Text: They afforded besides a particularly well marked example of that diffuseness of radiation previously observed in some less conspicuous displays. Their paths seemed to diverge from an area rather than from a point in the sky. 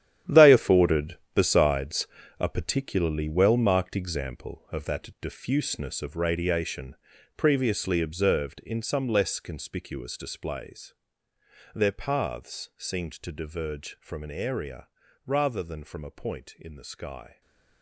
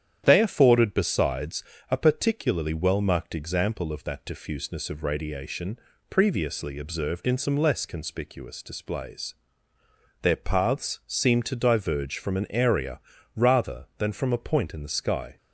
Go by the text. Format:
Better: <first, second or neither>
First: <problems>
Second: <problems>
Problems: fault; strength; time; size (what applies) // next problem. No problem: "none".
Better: second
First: gets quieter; strong; throughout; 12.5 dB // starts louder than the rest; strong; until 1.4 s; 10.5 dB // pauses between "afforded" and "besides"; slight; at 1.1 s; 0.18 s long // pauses between "besides" and "a"; slight; at 2.0 s; 0.32 s long // pauses between "radiation" and "previously"; at 6.9 s; 0.42 s long // pauses between "area" and "rather"; at 14.8 s; 0.38 s long // stays silent after the last word; slight; from 17.2 s on; 0.6 s long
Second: starts louder than the rest; strong; until 1.2 s; 9.5 dB // pauses between "besides" and "a"; slight; at 1.6 s; 0.28 s long // pauses between "radiation" and "previously"; slight; at 5.7 s; 0.30 s long // pauses between "area" and "rather"; slight; at 12.9 s; 0.36 s long